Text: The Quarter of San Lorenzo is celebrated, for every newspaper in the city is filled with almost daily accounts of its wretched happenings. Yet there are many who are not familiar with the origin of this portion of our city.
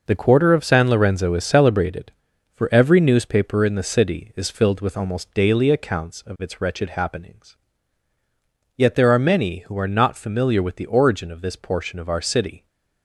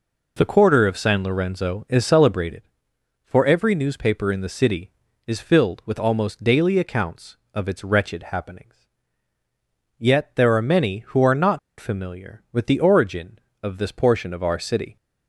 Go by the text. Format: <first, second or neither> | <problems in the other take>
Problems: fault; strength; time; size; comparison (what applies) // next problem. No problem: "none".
first | pauses between "not" and "familiar"; slight; at 11.5 s; 0.18 s long